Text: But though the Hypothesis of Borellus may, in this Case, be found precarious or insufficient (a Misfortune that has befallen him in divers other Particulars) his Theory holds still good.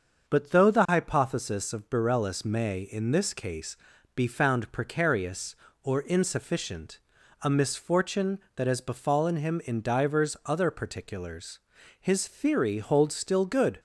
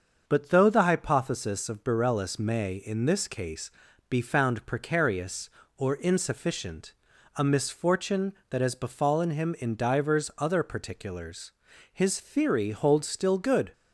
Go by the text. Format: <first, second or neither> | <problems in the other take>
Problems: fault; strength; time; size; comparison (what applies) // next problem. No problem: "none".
neither | starts louder than the rest; the same in both